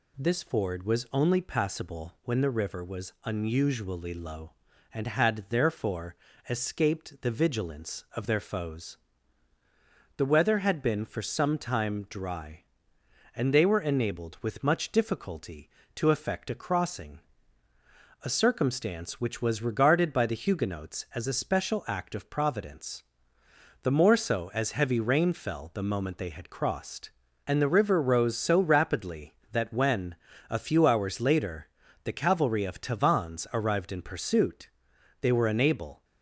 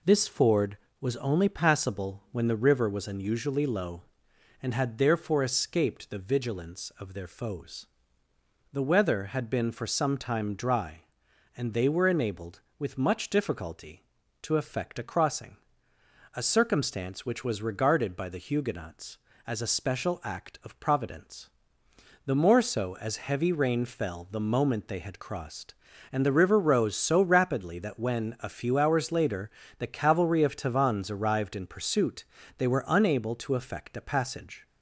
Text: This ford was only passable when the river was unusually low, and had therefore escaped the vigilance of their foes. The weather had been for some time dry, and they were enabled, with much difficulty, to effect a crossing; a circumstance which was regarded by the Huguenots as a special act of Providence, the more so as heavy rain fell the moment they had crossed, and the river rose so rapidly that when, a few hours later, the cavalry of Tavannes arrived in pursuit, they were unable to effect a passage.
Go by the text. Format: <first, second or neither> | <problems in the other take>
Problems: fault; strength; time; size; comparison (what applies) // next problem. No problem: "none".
second | pauses between "therefore" and "escaped"; slight; at 6.1 s; 0.34 s long // stops before "to effect a passage"; at 36.0 s